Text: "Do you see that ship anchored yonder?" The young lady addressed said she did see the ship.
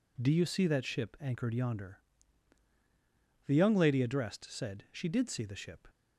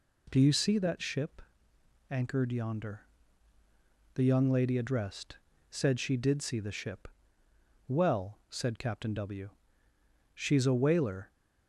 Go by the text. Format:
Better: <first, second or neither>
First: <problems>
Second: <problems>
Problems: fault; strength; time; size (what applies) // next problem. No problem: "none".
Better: first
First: none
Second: pauses between "ship" and "anchored"; noticeable; at 1.4 s; 0.70 s long // pauses between "addressed" and "said"; slight; at 5.3 s; 0.34 s long // goes on to say "Well said Captain W she's a whaler"; strong; from 7.8 s on; 3.4 s long